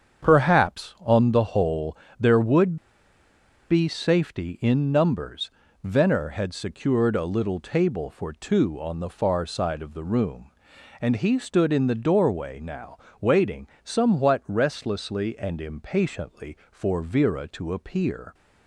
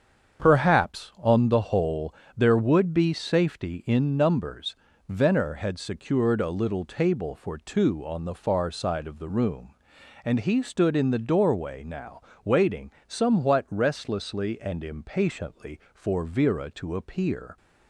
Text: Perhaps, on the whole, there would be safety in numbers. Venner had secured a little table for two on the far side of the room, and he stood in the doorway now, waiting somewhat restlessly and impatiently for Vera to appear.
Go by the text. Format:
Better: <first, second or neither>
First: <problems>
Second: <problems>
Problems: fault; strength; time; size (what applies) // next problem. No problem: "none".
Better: second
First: starts louder than the rest; strong; until 1.3 s; 7.5 dB // pauses between "would" and "be"; noticeable; at 2.7 s; 0.92 s long // pauses between "waiting" and "somewhat"; slight; at 13.6 s; 0.16 s long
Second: starts louder than the rest; strong; until 1.4 s; 7.5 dB // pauses between "waiting" and "somewhat"; slight; at 12.8 s; 0.16 s long